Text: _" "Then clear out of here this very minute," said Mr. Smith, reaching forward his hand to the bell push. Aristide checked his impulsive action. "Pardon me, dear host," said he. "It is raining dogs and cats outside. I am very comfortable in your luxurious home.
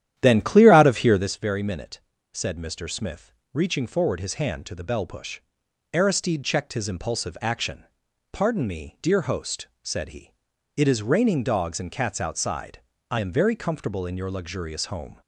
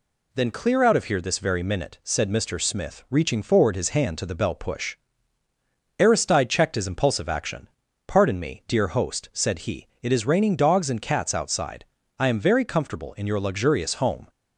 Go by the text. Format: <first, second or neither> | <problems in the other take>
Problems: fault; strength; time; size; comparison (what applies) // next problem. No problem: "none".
second | starts louder than the rest; strong; until 1.4 s; 11 dB